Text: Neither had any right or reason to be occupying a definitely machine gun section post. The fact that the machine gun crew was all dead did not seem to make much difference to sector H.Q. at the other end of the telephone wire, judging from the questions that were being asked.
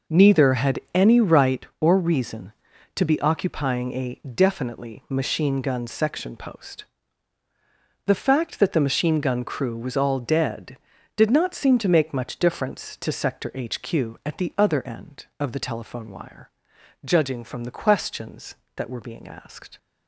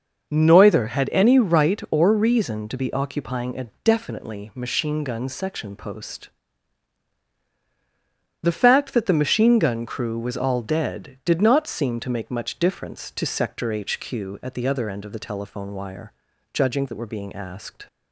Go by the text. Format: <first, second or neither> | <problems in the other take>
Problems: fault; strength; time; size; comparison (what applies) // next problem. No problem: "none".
first | skips "from the questions"; at 16.8 s